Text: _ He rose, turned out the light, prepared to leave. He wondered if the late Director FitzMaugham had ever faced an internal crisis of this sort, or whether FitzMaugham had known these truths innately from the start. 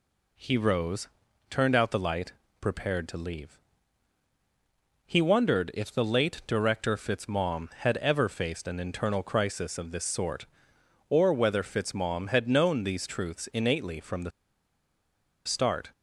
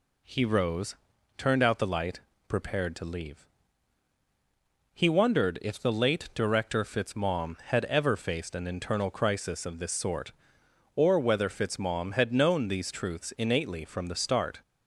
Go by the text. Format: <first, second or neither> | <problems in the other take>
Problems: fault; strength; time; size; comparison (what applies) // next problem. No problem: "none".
second | pauses between "the" and "start"; at 14.3 s; 1.1 s long